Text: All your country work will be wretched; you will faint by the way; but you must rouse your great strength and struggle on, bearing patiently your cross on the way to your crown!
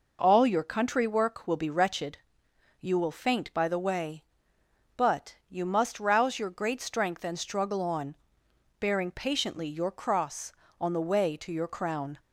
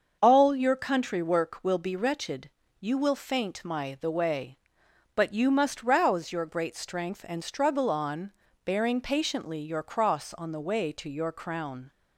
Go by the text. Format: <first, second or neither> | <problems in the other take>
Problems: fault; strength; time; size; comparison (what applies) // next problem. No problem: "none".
first | starts louder than the rest; until 1.2 s; 6.5 dB // says "my" for "by"; at 3.6 s